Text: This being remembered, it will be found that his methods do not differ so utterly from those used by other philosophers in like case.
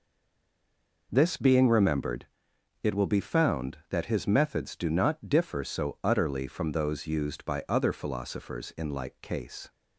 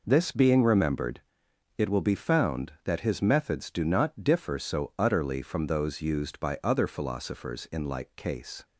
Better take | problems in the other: second | stays silent before the first word; until 1.0 s; 1.0 s long

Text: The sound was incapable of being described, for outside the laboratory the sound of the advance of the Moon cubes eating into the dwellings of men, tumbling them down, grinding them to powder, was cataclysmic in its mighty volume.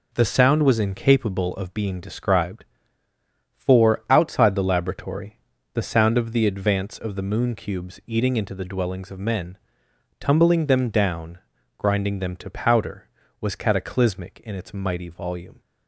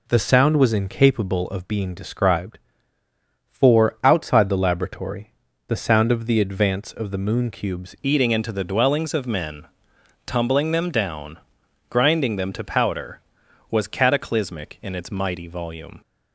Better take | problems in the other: first | pauses between "laboratory" and "the"; slight; at 5.3 s; 0.32 s long; slight in the first // changes voice at "eating"; from 8.0 s on; 8.0 s long

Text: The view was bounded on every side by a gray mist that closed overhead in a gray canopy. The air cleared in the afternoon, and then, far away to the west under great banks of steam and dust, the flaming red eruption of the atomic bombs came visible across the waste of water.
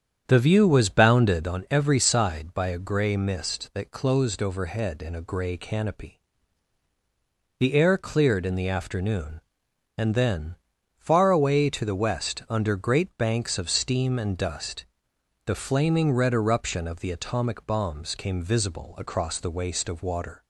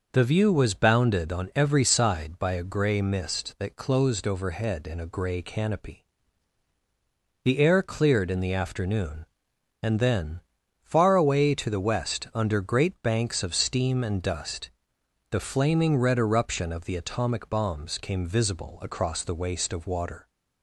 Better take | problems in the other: second | starts louder than the rest; strong; until 1.6 s; 8 dB

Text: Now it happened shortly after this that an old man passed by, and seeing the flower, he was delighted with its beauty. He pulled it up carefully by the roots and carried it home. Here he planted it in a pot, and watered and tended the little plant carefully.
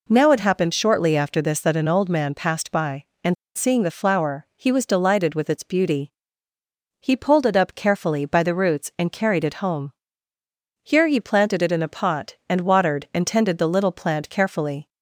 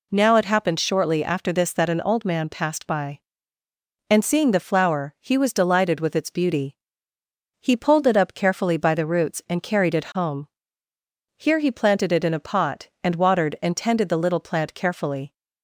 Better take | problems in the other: second | pauses between "and" and "seeing"; slight; at 3.3 s; 0.21 s long

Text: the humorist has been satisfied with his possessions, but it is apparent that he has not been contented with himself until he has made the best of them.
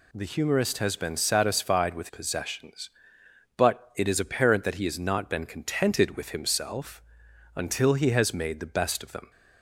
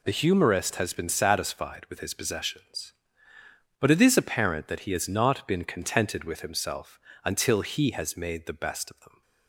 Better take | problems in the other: second | skips "his"; at 2.0 s // pauses between "himself" and "until"; noticeable; at 7.0 s; 0.54 s long; slight in the second

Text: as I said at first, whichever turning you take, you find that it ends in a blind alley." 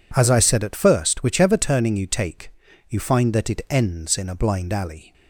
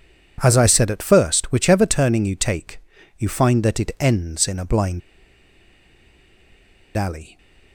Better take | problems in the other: first | pauses between "blind" and "alley"; strong; at 5.0 s; 1.9 s long

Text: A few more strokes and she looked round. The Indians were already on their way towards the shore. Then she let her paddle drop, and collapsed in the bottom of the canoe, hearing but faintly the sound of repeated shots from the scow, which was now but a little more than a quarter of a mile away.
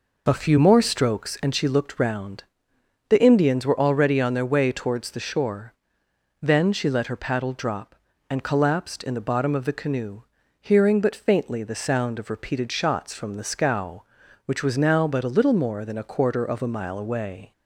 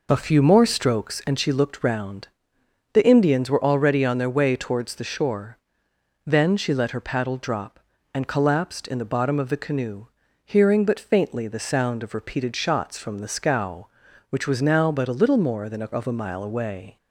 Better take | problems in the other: first | skips "quarter"; at 15.9 s

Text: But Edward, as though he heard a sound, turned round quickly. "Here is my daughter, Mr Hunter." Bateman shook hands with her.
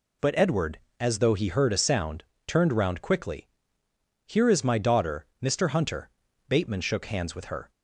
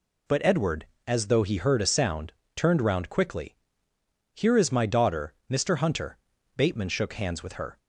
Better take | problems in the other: neither | none

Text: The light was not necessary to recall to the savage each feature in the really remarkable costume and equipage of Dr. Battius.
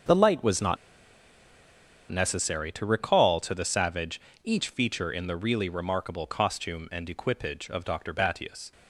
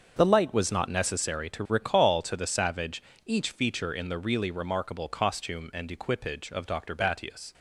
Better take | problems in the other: second | starts louder than the rest; until 2.4 s; 7 dB; also in the second // pauses between "not" and "necessary"; strong; at 0.7 s; 1.3 s long // pauses between "savage" and "each"; slight; at 4.1 s; 0.24 s long; slight in the second

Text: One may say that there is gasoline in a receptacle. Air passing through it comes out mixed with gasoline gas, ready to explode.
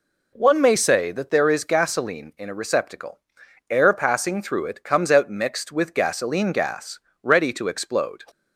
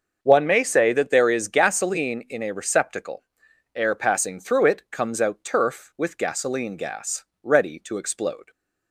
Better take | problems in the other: first | starts louder than the rest; until 1.2 s; 6.5 dB // says "turf" for "mixed"; at 5.4 s

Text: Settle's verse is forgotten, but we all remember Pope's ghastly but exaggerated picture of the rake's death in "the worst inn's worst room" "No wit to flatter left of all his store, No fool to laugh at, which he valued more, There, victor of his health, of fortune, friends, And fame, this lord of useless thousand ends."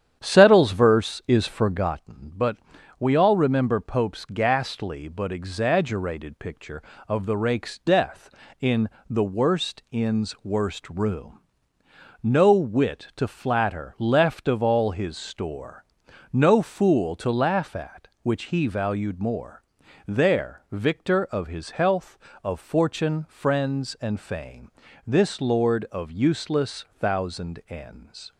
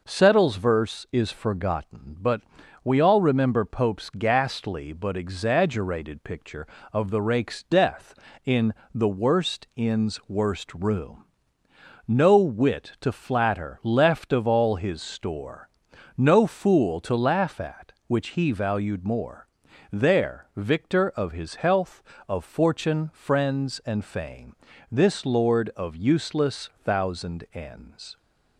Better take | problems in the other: second | starts louder than the rest; strong; until 1.9 s; 9.5 dB // pauses between "but" and "we"; at 2.5 s; 0.42 s long; also in the second // pauses between "in" and "the"; slight; at 8.8 s; 0.20 s long; slight in the second // pauses between "room" and "No"; noticeable; at 11.3 s; 0.82 s long; noticeable in the second // pauses between "useless" and "thousand"; slight; at 26.8 s; 0.16 s long; slight in the second

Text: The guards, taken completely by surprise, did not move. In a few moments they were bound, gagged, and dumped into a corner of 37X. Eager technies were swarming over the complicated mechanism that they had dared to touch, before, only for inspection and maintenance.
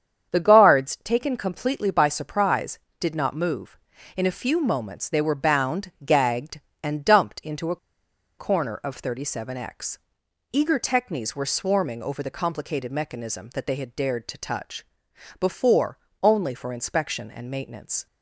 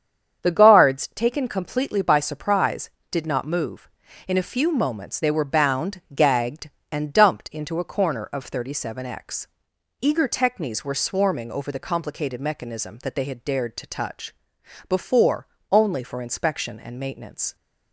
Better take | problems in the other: second | starts louder than the rest; strong; until 1.3 s; 8 dB; strong in the second // pauses between "a" and "corner"; noticeable; at 7.7 s; 0.62 s long

